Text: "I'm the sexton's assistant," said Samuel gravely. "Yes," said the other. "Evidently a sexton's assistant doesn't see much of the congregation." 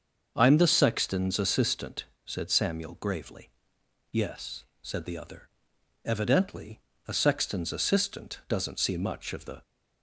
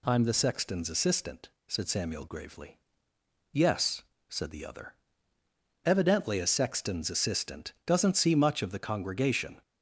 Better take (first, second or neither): second